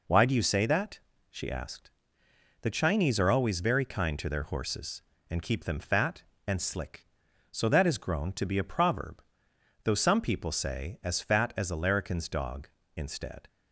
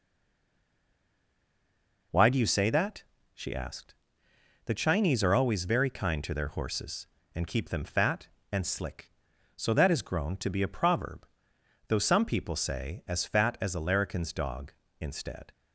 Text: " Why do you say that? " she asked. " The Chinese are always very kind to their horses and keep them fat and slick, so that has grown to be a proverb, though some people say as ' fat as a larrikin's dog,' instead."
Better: first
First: none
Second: stays silent before the first word; until 2.1 s; 2.1 s long

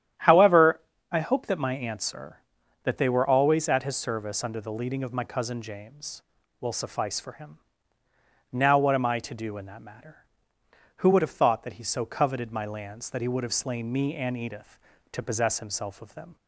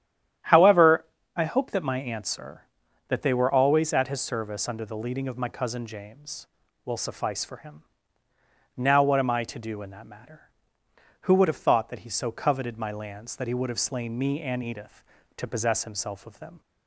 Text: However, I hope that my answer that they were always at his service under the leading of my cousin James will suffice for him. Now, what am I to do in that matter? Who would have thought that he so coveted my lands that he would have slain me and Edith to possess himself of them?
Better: neither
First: starts louder than the rest; strong; until 1.4 s; 10.5 dB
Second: starts louder than the rest; strong; until 1.7 s; 10.5 dB

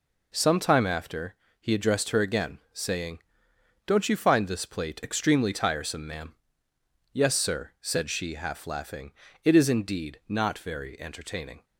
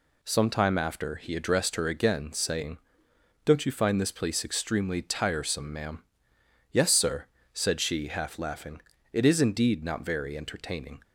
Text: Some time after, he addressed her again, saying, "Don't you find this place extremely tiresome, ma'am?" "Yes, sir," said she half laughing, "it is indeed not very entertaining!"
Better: second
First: says "plate" for "place"; at 4.6 s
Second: none

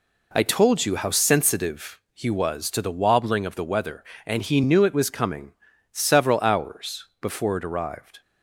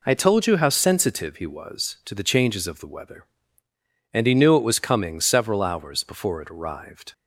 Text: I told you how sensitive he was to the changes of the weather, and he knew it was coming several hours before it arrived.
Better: second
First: says "wobbling" for "changes"; at 2.9 s // pauses between "coming" and "several"; at 5.5 s; 0.38 s long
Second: none

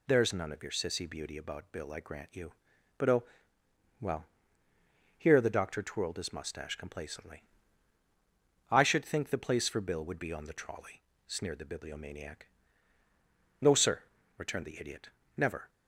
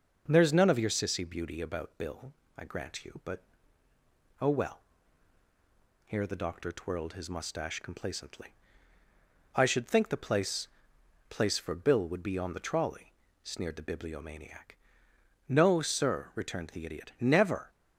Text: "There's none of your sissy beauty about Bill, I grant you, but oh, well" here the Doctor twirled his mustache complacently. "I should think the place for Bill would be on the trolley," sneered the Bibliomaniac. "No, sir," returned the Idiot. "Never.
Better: first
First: pauses between "well" and "here"; noticeable; at 4.2 s; 0.92 s long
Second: pauses between "but" and "oh"; noticeable; at 3.4 s; 0.98 s long // pauses between "well" and "here"; at 4.8 s; 1.2 s long // says "place" twice; at 11.2 s

